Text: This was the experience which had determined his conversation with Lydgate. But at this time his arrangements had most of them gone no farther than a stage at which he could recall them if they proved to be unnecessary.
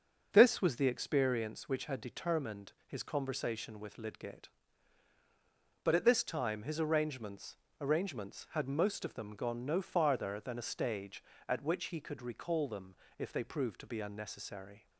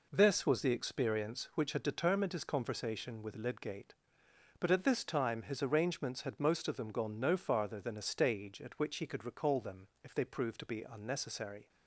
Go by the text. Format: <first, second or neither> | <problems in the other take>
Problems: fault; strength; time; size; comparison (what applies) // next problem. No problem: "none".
second | starts louder than the rest; until 1.3 s; 6 dB // says "arrangements" twice; at 7.8 s // pauses between "them" and "if"; slight; at 12.9 s; 0.24 s long